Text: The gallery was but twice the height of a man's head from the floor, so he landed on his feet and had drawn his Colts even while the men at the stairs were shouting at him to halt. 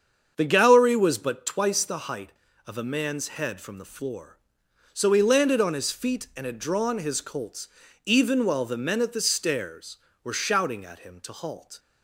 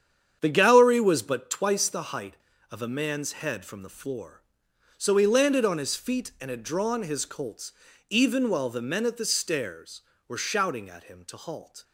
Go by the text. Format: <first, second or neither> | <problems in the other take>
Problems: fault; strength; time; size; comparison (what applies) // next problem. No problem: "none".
first | gets quieter; strong; throughout; 9 dB // starts louder than the rest; strong; until 1.4 s; 8.5 dB; strong in the first // pauses between "Colts" and "even"; slight; at 7.7 s; 0.36 s long; slight in the first